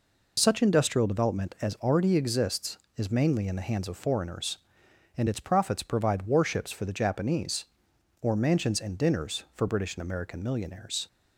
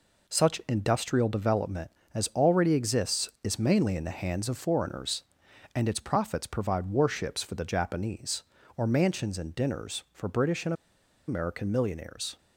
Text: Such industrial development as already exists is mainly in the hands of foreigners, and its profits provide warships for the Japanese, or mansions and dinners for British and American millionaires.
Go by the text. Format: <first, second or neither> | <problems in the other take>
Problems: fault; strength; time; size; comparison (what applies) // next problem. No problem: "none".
first | pauses between "and" and "American"; noticeable; at 10.7 s; 0.54 s long